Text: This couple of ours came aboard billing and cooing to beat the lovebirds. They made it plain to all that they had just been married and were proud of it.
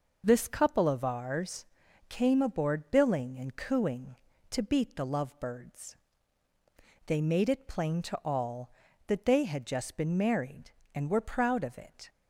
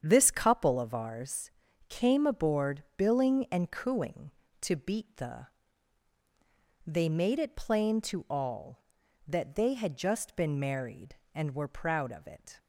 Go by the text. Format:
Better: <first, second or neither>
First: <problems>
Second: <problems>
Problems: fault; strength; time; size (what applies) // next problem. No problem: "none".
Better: first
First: pauses between "ours" and "came"; at 1.6 s; 0.42 s long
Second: starts louder than the rest; strong; until 1.0 s; 8 dB // pauses between "ours" and "came"; at 1.5 s; 0.38 s long // skips "lovebirds"; at 6.1 s